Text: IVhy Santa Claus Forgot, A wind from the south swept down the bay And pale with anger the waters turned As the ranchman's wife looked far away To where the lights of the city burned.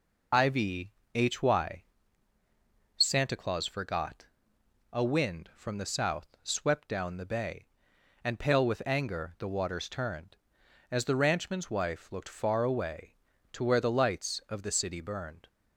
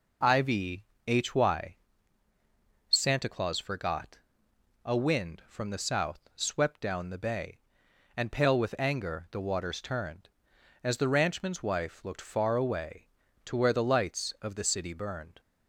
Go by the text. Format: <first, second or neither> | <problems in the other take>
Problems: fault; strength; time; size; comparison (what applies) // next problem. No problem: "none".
second | loses the start of "IVhy"; at 0.3 s; 40 ms // pauses between "IVhy" and "Santa"; strong; at 0.9 s; 2.0 s long; strong in the second // pauses between "south" and "swept"; slight; at 6.2 s; 0.16 s long; slight in the second